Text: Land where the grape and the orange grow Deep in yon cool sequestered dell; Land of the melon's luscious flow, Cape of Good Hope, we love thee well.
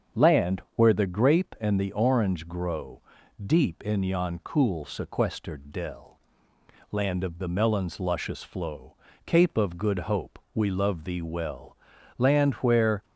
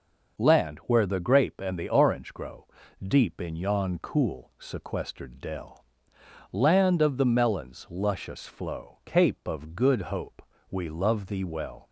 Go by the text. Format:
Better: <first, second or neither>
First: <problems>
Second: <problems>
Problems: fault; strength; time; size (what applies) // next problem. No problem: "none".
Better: second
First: starts louder than the rest; strong; until 1.2 s; 7.5 dB // pauses between "grow" and "Deep"; at 3.0 s; 0.44 s long // goes on to say "Land where"; noticeable; from 12.1 s on; 0.86 s long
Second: starts louder than the rest; noticeable; until 1.4 s; 6 dB // pauses between "grow" and "Deep"; slight; at 2.6 s; 0.34 s long